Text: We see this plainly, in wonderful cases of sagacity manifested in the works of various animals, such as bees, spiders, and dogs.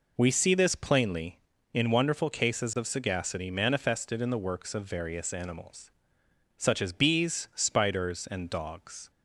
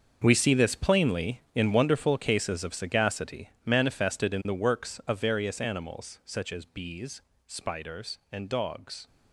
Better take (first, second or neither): first